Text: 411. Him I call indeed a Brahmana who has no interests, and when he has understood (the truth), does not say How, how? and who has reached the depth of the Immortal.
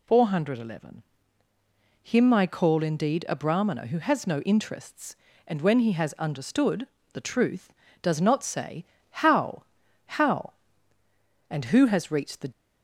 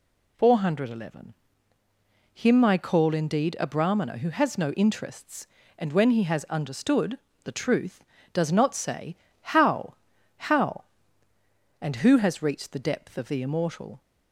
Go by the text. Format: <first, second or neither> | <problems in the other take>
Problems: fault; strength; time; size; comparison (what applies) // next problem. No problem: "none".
second | pauses between "say" and "How"; slight; at 8.8 s; 0.26 s long; slight in the second // stops before "depth of the Immortal"; at 12.5 s